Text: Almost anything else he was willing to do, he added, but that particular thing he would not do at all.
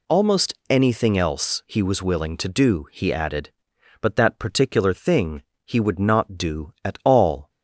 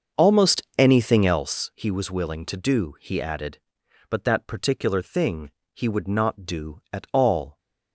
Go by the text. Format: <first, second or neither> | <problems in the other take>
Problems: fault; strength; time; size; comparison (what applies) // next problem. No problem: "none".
first | starts louder than the rest; until 1.5 s; 6.5 dB // pauses between "Almost" and "anything"; slight; at 0.6 s; 0.16 s long; slight in the first // pauses between "thing" and "he"; slight; at 5.4 s; 0.24 s long; slight in the first